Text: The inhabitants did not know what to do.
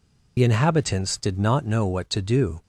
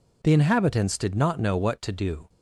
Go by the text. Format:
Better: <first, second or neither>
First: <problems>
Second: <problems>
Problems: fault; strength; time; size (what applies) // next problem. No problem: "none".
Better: second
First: loses the start of "The"; at 0.3 s; 50 ms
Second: none